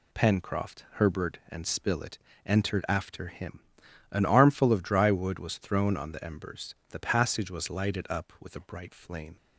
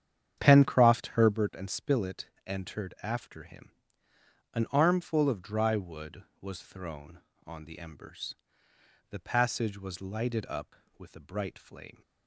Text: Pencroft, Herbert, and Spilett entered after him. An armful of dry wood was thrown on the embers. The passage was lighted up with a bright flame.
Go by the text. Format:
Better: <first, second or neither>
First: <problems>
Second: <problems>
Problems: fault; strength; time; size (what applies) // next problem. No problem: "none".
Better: first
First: pauses between "Spilett" and "entered"; slight; at 2.1 s; 0.26 s long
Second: starts louder than the rest; strong; until 1.4 s; 9 dB // pauses between "Spilett" and "entered"; slight; at 2.2 s; 0.18 s long